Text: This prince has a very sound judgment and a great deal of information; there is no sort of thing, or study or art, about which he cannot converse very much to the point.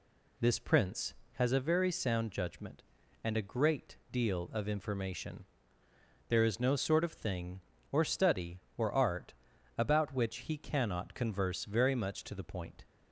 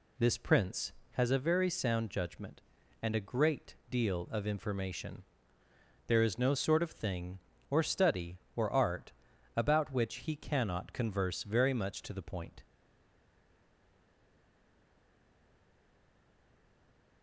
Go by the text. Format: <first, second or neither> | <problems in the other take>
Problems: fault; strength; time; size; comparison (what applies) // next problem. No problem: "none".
first | stays silent after the last word; strong; from 12.6 s on; 4.6 s long